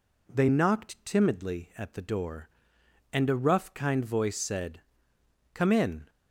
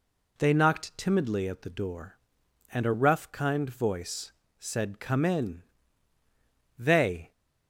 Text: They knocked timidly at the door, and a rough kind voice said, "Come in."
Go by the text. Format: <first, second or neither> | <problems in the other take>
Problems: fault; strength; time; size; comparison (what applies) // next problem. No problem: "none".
first | pauses between "voice" and "said"; slight; at 4.3 s; 0.26 s long // goes on to say "They"; from 6.7 s on; 0.54 s long